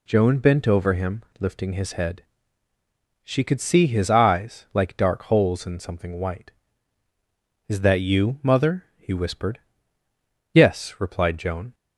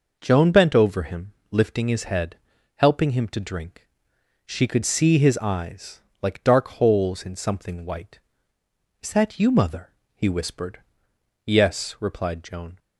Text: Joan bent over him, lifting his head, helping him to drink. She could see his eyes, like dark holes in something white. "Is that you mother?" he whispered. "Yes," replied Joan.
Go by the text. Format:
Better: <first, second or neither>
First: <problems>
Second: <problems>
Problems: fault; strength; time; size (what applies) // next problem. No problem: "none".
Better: second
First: skips "helping him to drink"; at 2.7 s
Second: none